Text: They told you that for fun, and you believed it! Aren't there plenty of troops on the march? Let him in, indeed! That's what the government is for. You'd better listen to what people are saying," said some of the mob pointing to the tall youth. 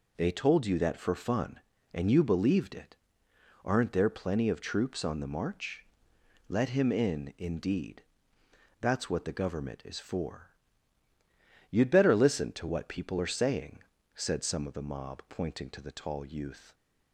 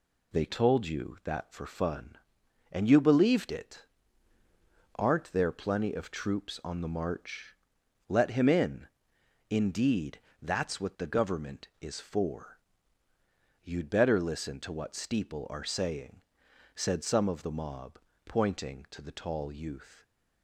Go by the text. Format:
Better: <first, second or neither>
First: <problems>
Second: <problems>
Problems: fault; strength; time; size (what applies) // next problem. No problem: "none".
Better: first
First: none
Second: says "steeple" for "people"; at 14.9 s // pauses between "mob" and "pointing"; slight; at 17.9 s; 0.28 s long // stays silent after the last word; slight; from 19.9 s on; 0.5 s long